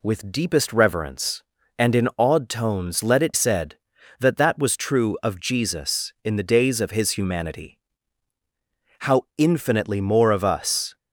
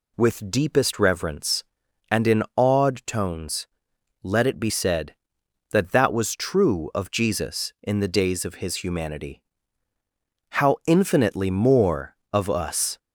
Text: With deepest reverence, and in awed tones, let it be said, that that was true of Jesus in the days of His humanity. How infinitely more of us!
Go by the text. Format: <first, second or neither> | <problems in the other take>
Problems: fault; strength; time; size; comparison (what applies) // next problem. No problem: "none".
second | skips "be"; at 3.3 s // pauses between "How" and "infinitely"; slight; at 9.2 s; 0.16 s long